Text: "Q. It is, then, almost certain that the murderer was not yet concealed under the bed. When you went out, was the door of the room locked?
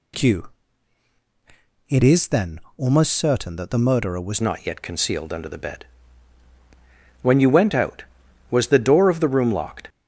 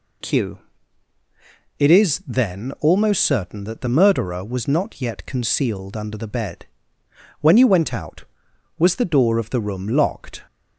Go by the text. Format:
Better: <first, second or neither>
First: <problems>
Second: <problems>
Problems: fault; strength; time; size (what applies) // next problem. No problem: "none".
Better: second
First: changes voice at "not"; from 4.4 s on; 5.4 s long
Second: none